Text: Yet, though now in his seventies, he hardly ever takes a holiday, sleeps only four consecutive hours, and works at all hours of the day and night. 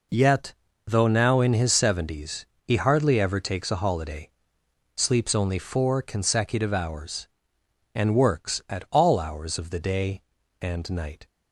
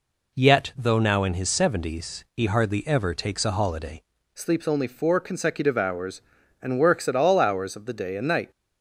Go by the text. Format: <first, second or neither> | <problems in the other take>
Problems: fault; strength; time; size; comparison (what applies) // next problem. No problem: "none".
first | changes voice at "sleeps"; from 4.3 s on; 4.2 s long